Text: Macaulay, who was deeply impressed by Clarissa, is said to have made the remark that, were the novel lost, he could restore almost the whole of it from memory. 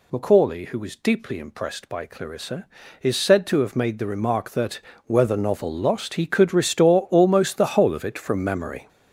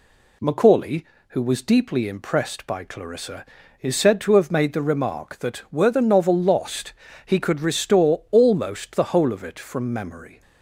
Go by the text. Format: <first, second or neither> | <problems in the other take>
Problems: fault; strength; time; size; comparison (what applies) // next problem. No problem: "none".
second | gets louder; strong; throughout; 8.5 dB